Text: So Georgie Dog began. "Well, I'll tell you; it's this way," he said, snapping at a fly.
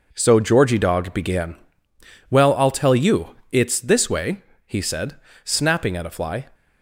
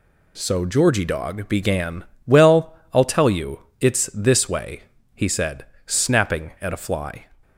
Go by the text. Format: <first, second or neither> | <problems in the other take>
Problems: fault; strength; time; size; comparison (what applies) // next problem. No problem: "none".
second | gets quieter; strong; throughout; 8 dB